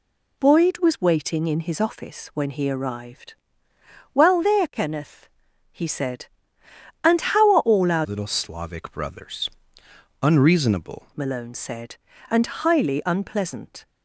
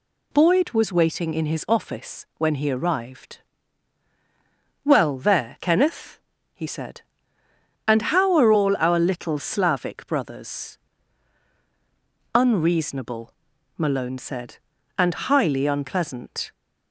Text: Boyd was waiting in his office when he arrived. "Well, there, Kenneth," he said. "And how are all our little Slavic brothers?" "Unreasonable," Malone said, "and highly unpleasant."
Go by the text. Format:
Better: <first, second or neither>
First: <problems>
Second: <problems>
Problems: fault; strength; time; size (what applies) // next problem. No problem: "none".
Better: second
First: changes voice from "little" to "Unreasonable"; from 8.0 to 11.0 s; 3.0 s long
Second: none